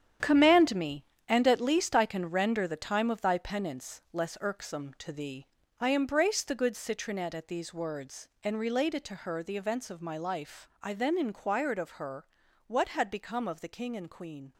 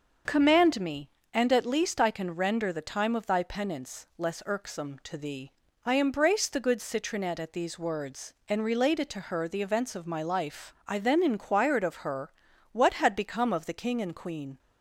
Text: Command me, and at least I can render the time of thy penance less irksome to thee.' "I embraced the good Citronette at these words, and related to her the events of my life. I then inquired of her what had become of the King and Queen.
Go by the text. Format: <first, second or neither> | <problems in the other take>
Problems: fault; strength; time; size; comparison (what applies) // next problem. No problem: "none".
second | gets quieter; strong; throughout; 10.5 dB // pauses between "her" and "what"; at 12.2 s; 0.40 s long; also in the second